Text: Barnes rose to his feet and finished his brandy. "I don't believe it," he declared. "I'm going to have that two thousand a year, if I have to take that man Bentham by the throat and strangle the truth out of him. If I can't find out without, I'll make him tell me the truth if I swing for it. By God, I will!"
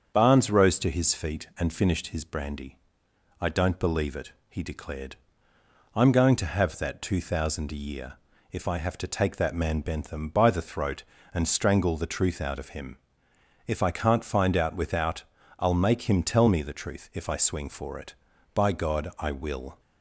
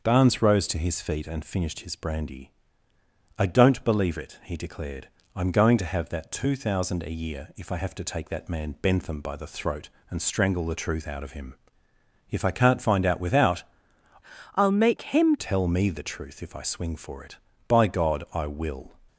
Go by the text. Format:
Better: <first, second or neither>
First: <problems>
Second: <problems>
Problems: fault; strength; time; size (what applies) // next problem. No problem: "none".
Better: first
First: starts louder than the rest; strong; until 1.1 s; 7.5 dB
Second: starts louder than the rest; until 1.0 s; 6.5 dB // changes voice from "I'll" to "him"; from 14.5 to 15.3 s; 0.8 s long